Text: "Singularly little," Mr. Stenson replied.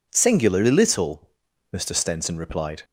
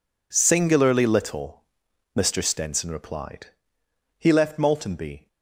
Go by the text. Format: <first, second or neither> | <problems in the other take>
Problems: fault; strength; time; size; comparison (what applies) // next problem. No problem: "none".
first | goes on to say "He left Maltenby"; noticeable; from 4.1 s on; 1.1 s long